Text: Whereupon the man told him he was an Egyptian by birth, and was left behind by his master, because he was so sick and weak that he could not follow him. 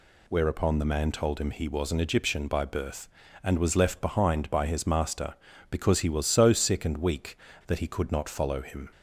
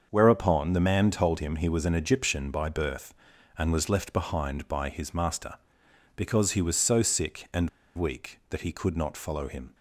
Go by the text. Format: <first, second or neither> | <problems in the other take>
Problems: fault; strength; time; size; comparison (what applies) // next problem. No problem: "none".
first | starts louder than the rest; until 1.1 s; 6.5 dB // pauses between "and" and "weak"; slight; at 7.6 s; 0.26 s long